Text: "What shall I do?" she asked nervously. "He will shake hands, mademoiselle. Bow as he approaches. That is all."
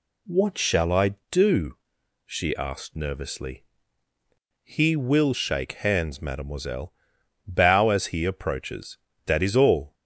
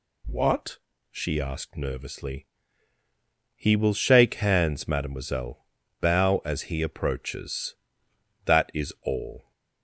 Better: first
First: none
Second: skips "shall I do"; at 0.9 s

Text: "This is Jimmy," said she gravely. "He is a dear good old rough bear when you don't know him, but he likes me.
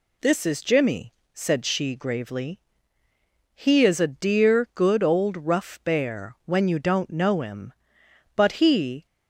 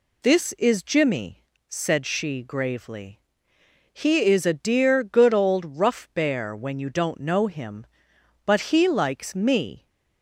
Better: second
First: stops before "likes me"; at 9.0 s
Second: none

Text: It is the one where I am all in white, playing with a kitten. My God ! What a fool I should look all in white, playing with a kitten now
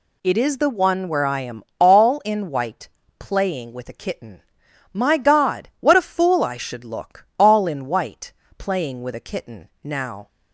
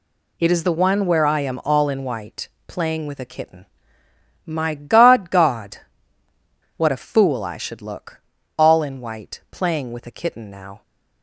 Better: first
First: none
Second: says "God" twice; at 5.3 s // pauses between "look" and "all"; slight; at 8.2 s; 0.36 s long

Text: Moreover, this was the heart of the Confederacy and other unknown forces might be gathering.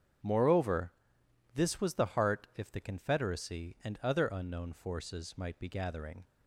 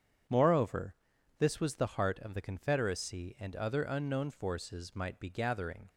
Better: second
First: starts louder than the rest; strong; until 1.8 s; 7.5 dB // says "if" for "of"; at 2.5 s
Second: starts louder than the rest; strong; until 1.7 s; 8 dB

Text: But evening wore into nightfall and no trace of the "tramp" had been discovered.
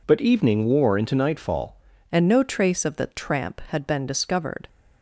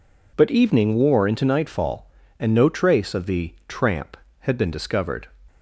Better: second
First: changes voice at "and"; from 2.0 s on; 2.6 s long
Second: none

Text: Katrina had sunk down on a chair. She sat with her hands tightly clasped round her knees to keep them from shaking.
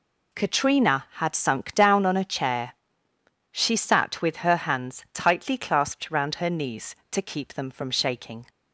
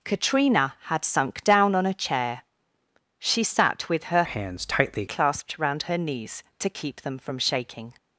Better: first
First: none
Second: changes voice from "hands" to "tightly"; from 4.2 to 5.0 s; 0.8 s long

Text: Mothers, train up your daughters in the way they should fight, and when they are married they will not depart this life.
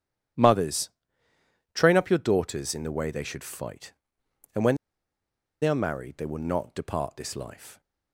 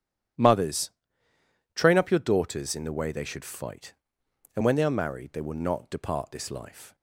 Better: second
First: starts louder than the rest; strong; until 2.2 s; 11 dB // pauses between "when" and "they"; noticeable; at 4.7 s; 0.86 s long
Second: starts louder than the rest; strong; until 2.2 s; 11 dB

